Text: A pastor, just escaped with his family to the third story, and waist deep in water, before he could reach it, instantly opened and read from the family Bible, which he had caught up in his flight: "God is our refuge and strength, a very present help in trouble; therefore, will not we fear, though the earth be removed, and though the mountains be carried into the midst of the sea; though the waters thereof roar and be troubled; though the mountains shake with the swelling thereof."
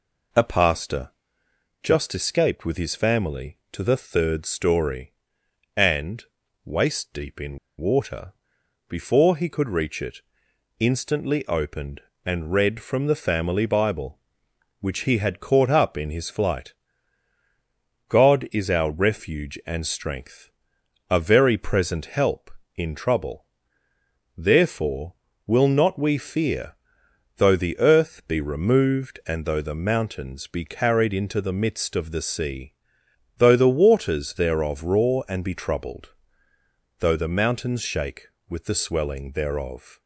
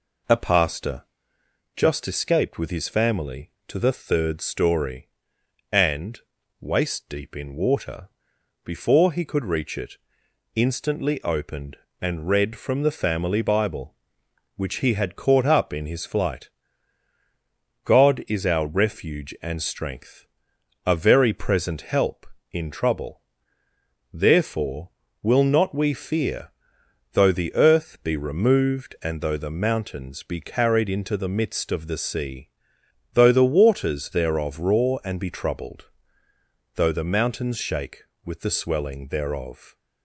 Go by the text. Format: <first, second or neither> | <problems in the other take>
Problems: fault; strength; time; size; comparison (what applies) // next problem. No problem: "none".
second | pauses between "and" and "waist"; at 6.2 s; 0.40 s long; also in the second // pauses between "in" and "water"; slight; at 7.5 s; 0.20 s long